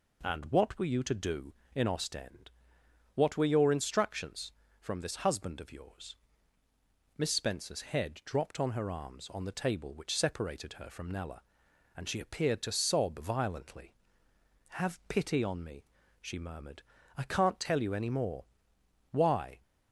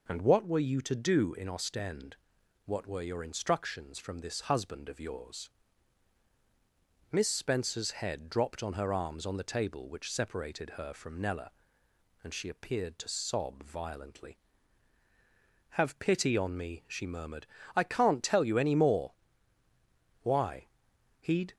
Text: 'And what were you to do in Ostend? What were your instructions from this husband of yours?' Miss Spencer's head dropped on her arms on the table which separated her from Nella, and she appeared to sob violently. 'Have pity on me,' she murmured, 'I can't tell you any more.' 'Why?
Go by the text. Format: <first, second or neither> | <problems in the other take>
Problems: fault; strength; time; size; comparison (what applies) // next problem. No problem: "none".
first | goes on to say "He'd"; slight; from 21.1 s on; 0.34 s long